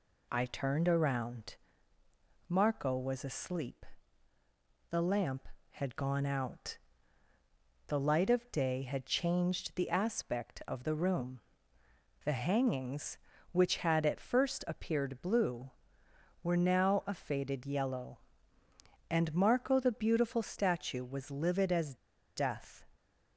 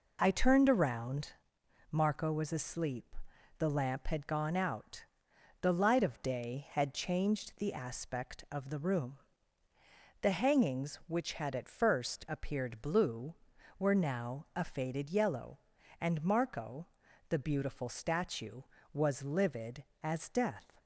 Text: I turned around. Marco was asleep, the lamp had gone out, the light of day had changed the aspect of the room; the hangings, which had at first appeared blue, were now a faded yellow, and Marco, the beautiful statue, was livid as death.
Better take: second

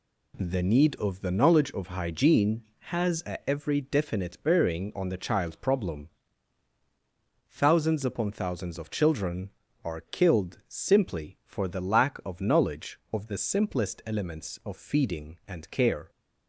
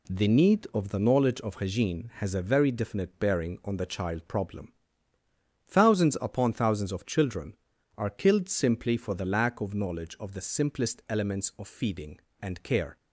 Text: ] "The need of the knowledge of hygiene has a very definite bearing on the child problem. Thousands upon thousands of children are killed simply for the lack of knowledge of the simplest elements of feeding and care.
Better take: second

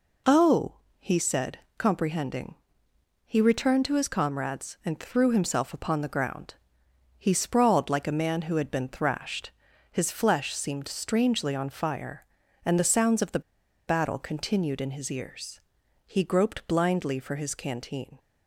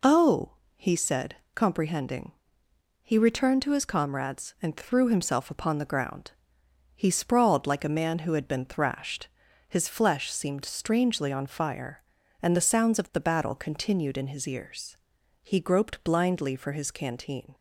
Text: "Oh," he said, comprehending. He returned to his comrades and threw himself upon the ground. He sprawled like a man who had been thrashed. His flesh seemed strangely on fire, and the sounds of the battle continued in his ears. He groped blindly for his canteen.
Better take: second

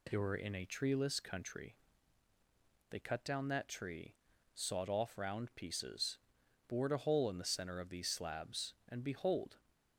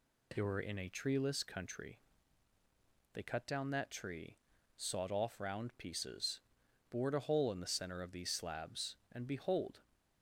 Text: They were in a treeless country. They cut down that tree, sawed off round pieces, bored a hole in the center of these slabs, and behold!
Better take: neither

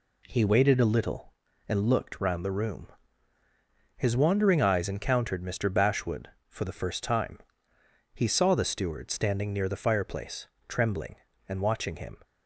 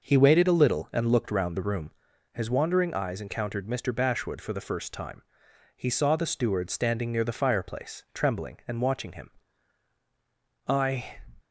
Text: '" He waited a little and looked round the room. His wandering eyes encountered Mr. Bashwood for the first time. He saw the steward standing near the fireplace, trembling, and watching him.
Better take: first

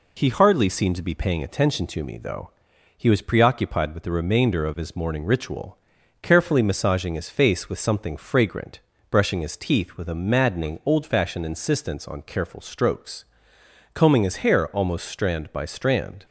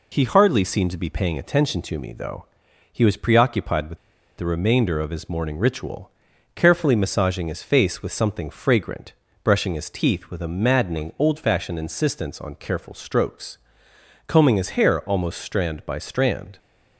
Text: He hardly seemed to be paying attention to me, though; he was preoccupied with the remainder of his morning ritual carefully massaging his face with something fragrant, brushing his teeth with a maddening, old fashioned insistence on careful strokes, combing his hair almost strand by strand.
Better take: first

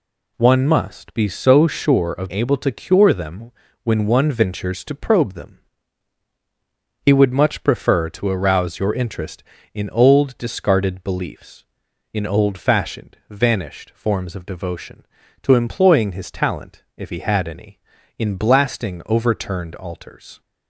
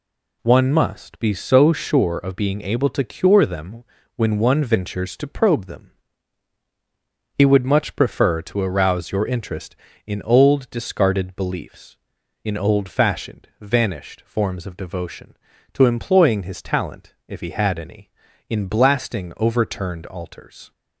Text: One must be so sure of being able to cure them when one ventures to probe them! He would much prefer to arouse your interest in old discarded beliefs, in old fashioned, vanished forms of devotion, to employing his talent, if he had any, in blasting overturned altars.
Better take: second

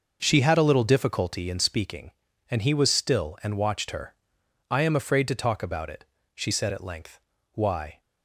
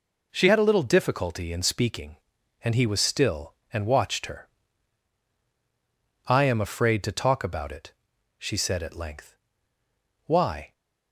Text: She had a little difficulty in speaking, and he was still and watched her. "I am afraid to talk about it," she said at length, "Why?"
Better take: second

